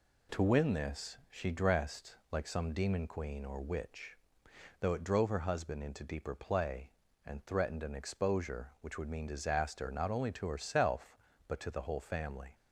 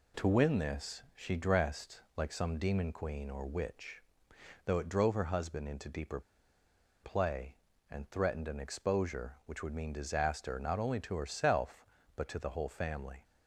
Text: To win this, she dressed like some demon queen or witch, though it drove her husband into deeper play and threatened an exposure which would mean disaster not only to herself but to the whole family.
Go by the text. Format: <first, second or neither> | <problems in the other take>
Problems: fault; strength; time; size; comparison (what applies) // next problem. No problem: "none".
first | pauses between "dressed" and "like"; slight; at 1.9 s; 0.16 s long; slight in the first // pauses between "deeper" and "play"; noticeable; at 6.2 s; 0.81 s long